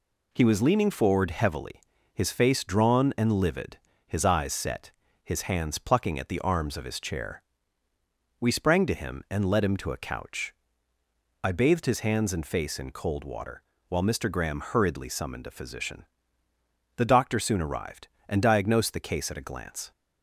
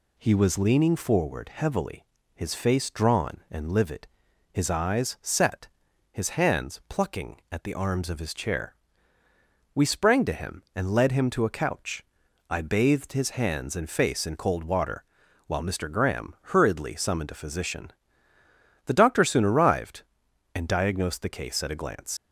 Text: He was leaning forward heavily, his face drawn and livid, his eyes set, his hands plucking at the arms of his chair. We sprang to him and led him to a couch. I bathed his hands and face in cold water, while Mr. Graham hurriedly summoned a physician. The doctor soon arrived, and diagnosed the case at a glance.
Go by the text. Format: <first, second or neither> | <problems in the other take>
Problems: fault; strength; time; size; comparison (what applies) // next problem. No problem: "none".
first | pauses between "Graham" and "hurriedly"; slight; at 16.3 s; 0.16 s long // leaves "glance" unfinished; at 22.1 s; 90 ms